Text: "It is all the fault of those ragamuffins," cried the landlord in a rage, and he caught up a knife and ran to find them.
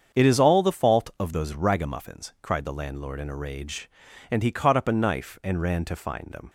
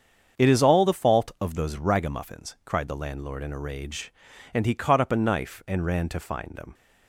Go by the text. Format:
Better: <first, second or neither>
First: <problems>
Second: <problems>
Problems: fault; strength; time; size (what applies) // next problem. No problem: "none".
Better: neither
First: starts louder than the rest; strong; until 1.2 s; 7.5 dB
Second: starts louder than the rest; strong; until 1.4 s; 7.5 dB